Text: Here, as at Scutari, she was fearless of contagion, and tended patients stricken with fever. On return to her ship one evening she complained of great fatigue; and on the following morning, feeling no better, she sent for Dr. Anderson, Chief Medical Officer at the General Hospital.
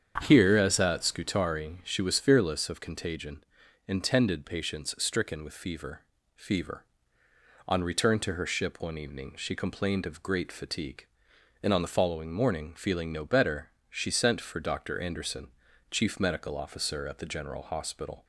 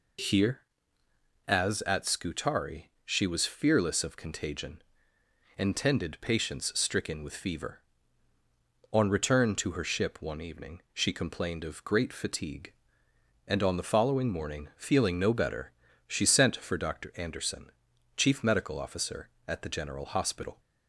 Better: second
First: starts louder than the rest; strong; until 1.2 s; 7.5 dB // says "fever" twice; at 6.3 s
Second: none

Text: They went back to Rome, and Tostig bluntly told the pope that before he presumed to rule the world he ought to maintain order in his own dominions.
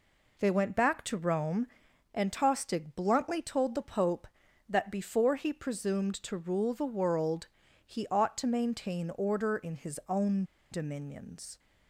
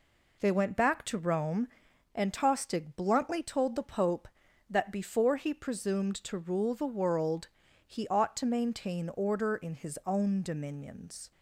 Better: second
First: pauses between "world" and "he"; at 7.4 s; 0.38 s long // pauses between "own" and "dominions"; slight; at 10.4 s; 0.28 s long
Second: pauses between "world" and "he"; at 7.4 s; 0.38 s long

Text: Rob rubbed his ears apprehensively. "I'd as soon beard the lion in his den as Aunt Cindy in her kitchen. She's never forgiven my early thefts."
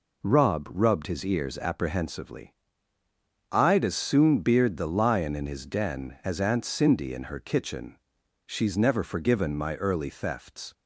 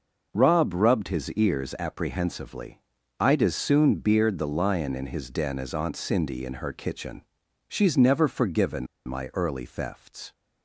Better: first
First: none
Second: pauses between "forgiven" and "my"; slight; at 8.8 s; 0.20 s long

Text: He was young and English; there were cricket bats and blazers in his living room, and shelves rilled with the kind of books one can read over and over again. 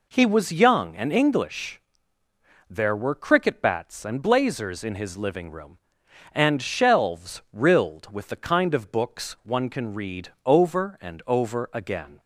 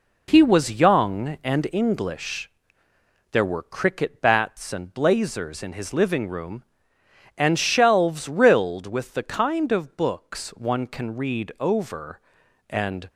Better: first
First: none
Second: stops before "over again"; at 13.0 s

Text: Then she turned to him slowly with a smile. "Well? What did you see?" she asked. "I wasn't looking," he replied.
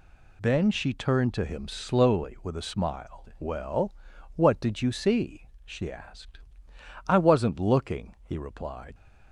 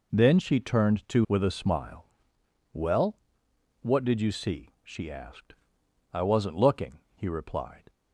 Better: first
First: none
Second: skips "him slowly"; at 1.2 s

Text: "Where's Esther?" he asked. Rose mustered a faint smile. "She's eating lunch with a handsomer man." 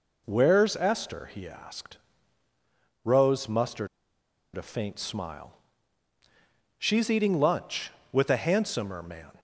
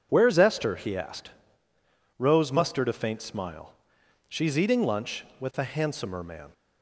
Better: second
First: pauses between "mustered" and "a"; noticeable; at 3.8 s; 0.68 s long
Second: none

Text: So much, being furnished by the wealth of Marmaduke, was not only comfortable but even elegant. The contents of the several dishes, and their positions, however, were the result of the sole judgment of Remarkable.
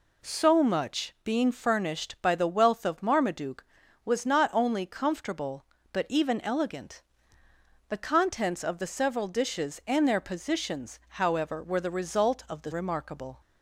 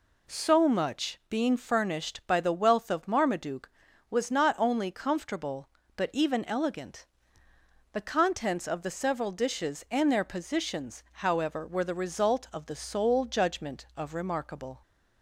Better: second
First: skips "sole judgment of"; at 12.7 s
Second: none

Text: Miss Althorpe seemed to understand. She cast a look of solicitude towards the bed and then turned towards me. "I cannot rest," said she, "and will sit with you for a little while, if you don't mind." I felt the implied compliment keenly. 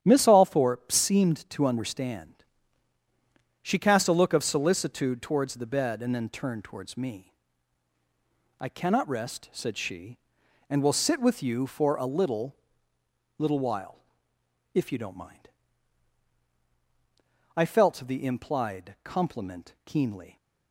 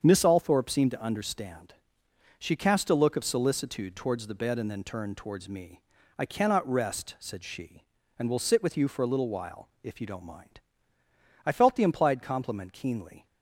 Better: second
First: starts louder than the rest; strong; until 1.0 s; 10 dB // says "little" twice; at 13.3 s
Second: starts louder than the rest; strong; until 1.0 s; 7 dB

